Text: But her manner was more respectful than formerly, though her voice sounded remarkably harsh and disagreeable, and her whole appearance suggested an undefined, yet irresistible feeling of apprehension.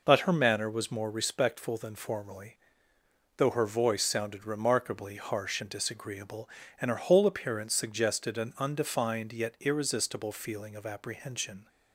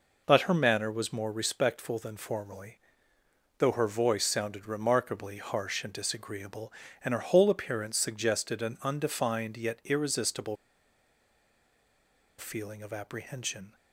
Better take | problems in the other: first | pauses between "irresistible" and "feeling"; strong; at 10.5 s; 1.8 s long

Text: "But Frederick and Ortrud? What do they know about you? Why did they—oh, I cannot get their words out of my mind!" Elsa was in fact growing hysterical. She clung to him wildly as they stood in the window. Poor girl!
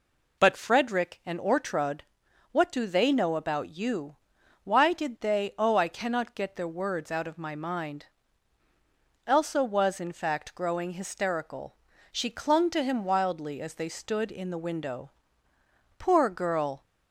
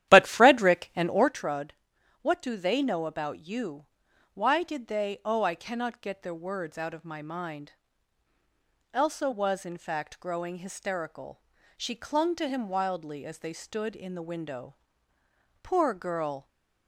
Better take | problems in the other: first | starts louder than the rest; strong; until 1.4 s; 12 dB

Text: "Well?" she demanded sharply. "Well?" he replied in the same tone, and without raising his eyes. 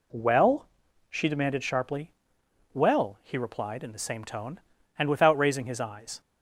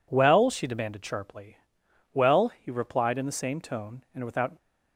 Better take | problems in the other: first | stops before "raising his eyes"; at 4.5 s

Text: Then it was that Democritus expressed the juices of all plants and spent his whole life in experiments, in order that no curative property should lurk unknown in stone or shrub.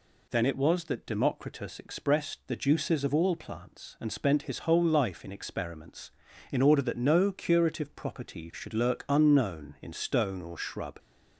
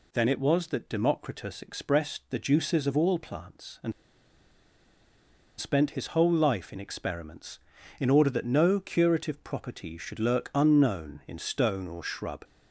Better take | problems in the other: first | pauses between "and" and "spent"; strong; at 3.9 s; 1.6 s long

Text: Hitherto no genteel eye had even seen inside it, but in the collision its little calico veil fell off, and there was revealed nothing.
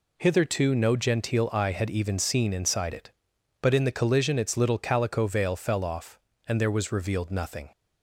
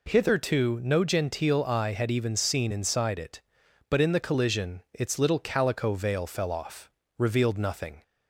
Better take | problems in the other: first | skips "and there was"; at 7.0 s

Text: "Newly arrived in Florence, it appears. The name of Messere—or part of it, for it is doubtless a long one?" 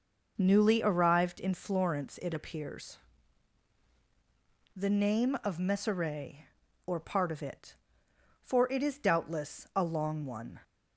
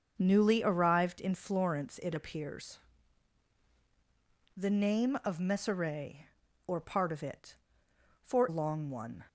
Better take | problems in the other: first | starts louder than the rest; until 1.1 s; 6.5 dB // skips "it is doubtless a"; at 8.4 s

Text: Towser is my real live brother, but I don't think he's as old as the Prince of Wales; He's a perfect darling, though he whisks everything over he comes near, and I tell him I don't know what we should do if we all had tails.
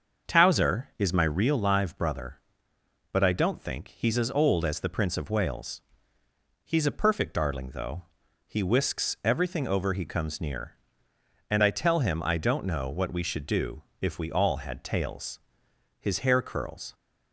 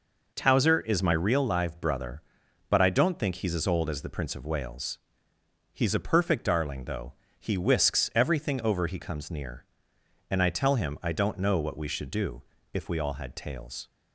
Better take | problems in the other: second | starts louder than the rest; until 1.3 s; 6.5 dB // pauses between "though" and "he"; at 8.0 s; 0.44 s long; slight in the second // pauses between "do" and "if"; slight; at 13.8 s; 0.18 s long; slight in the second // goes on to say "His hair curls"; noticeable; from 15.9 s on; 0.96 s long

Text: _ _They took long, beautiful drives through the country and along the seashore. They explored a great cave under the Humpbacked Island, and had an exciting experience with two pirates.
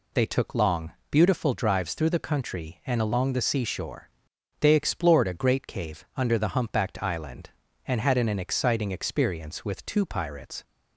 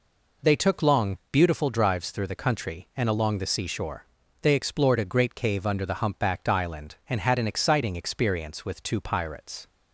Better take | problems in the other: second | says "an" twice; at 8.2 s

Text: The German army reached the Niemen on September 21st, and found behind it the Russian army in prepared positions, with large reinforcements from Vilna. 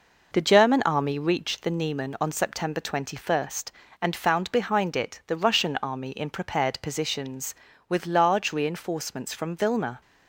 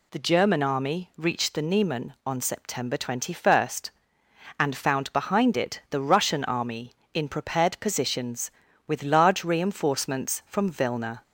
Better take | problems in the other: second | starts louder than the rest; noticeable; until 1.6 s; 5 dB

